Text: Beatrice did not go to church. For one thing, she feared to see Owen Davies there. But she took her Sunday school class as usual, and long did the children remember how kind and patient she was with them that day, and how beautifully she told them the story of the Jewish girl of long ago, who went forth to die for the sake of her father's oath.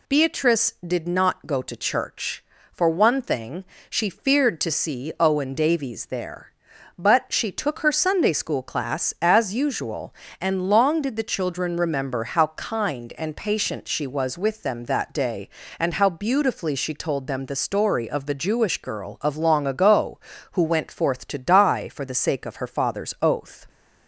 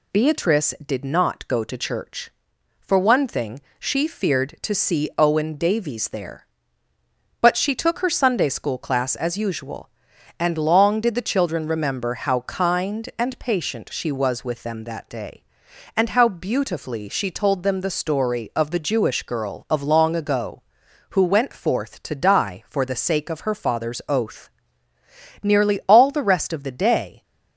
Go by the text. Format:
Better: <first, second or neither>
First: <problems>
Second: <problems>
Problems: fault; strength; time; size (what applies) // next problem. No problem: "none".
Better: first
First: none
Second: goes on to say "Nearly all the rest of the day"; strong; from 25.4 s on; 1.8 s long